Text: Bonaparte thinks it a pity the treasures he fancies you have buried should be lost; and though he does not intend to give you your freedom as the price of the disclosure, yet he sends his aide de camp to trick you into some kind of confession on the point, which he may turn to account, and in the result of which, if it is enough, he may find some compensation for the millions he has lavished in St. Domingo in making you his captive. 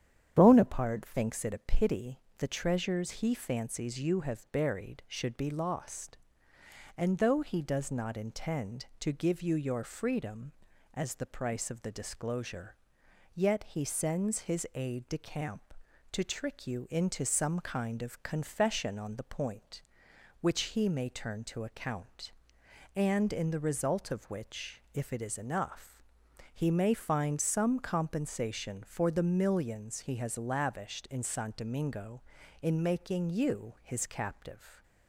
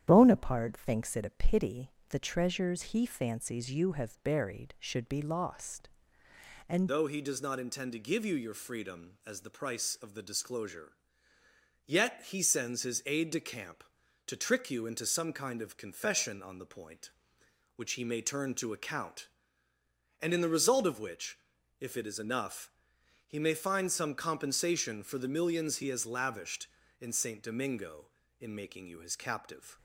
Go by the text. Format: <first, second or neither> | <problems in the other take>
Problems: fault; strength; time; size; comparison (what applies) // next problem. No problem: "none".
first | starts louder than the rest; strong; until 1.0 s; 10 dB; strong in the first // pauses between "pity" and "the"; slight; at 1.9 s; 0.18 s long; slight in the first // changes voice at "though"; from 6.8 s on; 22.9 s long